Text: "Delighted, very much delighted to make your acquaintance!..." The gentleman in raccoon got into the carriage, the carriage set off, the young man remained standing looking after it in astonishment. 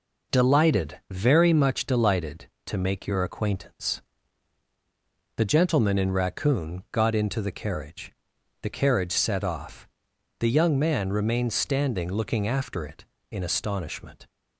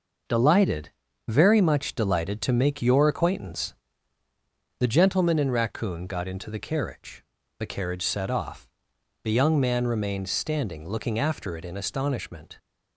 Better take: neither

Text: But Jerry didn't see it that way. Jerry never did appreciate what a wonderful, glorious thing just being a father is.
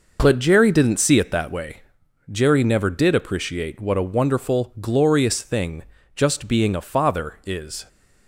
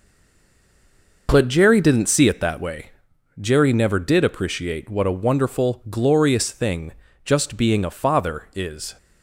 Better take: first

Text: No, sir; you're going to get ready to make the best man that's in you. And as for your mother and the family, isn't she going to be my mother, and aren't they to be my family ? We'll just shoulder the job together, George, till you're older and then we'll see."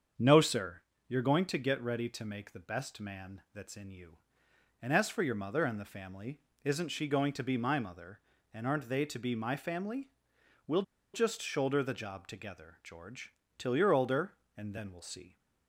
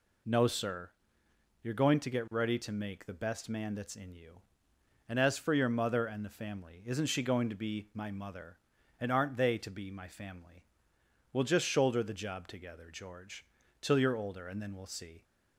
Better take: second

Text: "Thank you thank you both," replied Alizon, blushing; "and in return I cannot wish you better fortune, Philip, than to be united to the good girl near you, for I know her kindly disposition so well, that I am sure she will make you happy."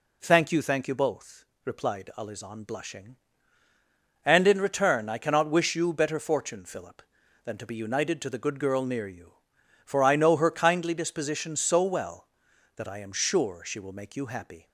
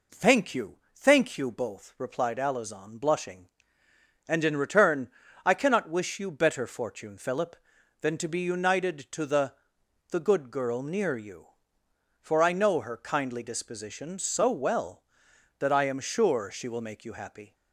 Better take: first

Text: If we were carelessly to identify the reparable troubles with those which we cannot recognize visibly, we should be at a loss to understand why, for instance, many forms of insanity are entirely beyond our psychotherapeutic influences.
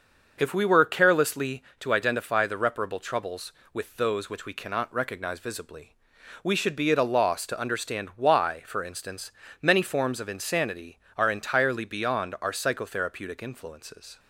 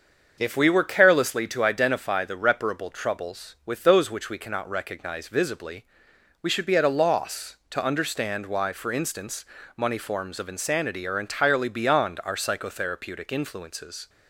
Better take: first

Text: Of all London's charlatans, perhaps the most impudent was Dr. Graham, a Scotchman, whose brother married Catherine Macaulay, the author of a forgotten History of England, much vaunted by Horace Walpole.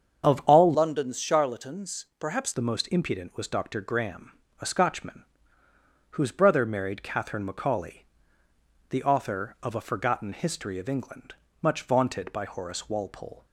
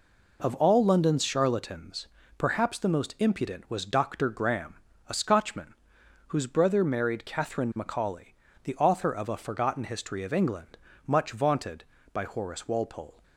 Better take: second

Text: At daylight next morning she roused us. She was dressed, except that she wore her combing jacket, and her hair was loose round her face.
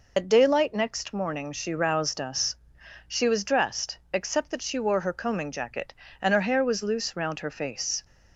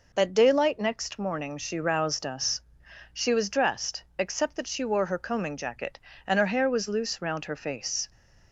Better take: second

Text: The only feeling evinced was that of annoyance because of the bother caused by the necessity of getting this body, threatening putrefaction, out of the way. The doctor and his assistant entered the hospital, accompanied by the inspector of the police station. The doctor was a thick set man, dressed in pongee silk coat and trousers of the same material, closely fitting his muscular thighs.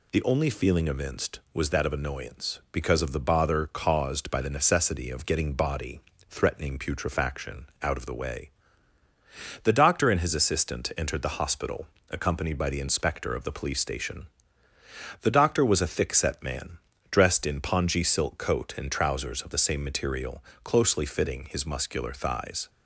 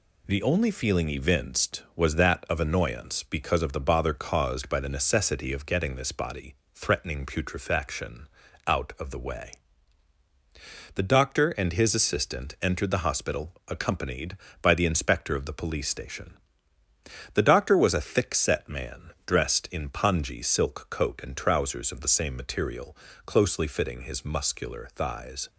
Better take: second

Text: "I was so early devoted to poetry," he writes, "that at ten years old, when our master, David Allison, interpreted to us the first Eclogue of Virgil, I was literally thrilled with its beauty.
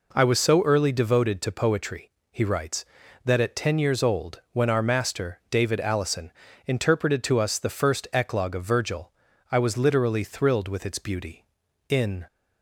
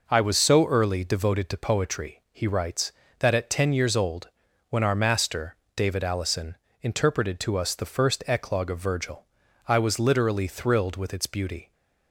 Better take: second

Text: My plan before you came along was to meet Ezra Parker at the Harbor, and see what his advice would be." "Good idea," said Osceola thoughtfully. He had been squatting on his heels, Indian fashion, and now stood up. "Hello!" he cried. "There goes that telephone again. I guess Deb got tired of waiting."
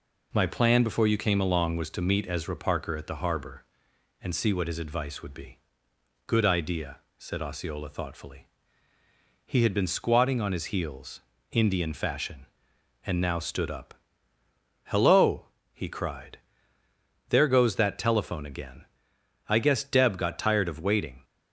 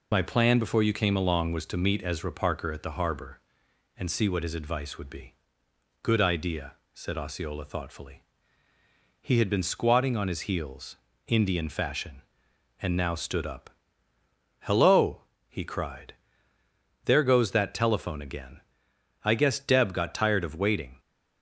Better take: first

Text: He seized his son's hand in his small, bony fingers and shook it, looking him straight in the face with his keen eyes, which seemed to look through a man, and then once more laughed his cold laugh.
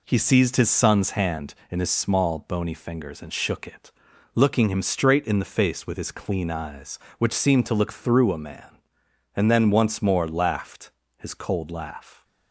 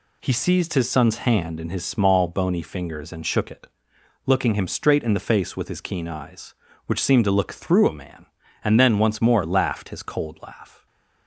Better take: second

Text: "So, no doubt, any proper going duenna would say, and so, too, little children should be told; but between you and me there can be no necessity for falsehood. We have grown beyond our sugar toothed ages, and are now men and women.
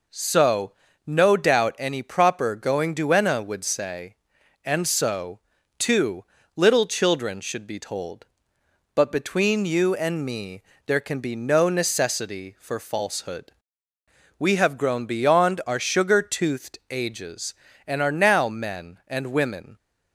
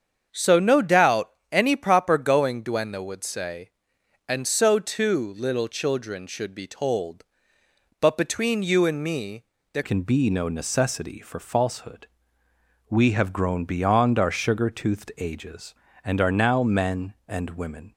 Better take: first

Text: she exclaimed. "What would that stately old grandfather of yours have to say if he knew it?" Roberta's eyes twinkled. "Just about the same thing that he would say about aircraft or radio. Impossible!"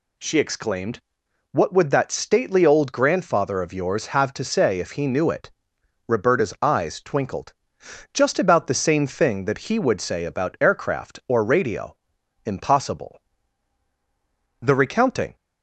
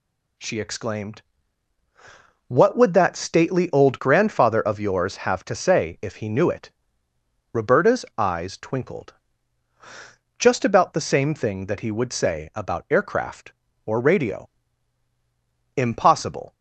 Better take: second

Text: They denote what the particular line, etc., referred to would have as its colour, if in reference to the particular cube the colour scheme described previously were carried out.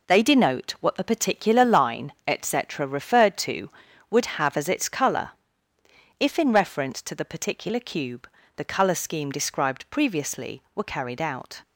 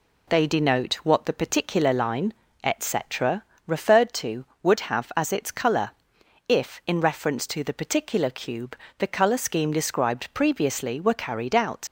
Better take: first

